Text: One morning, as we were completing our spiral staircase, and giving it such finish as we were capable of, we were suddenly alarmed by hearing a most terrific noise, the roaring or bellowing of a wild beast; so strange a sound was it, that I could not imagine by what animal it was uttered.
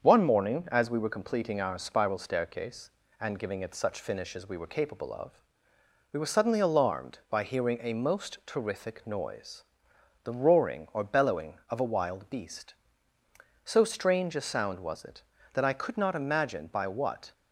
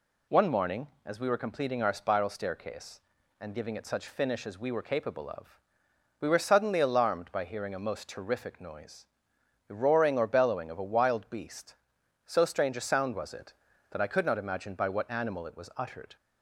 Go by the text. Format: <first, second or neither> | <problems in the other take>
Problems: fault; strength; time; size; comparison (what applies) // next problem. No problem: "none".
second | starts louder than the rest; until 1.0 s; 7 dB // stops before "animal it was uttered"; at 17.3 s